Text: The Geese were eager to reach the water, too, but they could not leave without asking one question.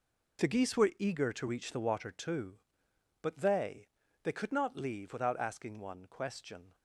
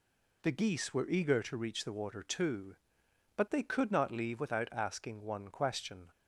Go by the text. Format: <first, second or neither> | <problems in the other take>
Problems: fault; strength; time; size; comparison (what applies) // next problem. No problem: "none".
second | says "they" twice; at 4.2 s